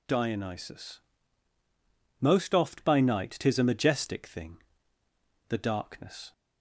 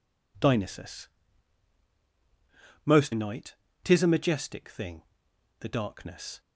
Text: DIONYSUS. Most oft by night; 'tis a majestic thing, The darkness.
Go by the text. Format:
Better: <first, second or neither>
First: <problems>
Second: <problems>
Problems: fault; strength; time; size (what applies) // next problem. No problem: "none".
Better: first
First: none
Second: skips "oft by"; at 3.1 s